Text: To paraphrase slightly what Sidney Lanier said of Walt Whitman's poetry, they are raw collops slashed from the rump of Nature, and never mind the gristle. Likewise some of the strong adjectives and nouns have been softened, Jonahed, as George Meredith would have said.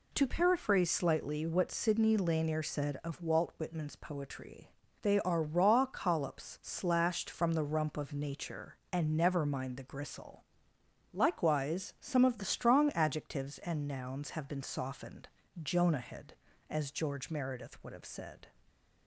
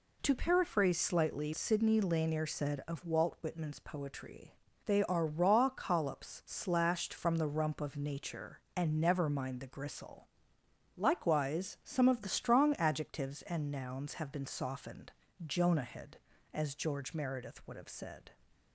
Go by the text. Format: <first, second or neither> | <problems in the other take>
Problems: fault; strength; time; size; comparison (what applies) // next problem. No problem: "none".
first | skips "what"; at 1.5 s